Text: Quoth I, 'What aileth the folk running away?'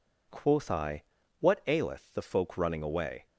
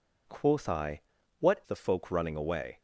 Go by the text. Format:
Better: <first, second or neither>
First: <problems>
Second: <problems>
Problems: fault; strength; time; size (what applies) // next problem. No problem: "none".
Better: first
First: none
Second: skips "aileth"; at 1.6 s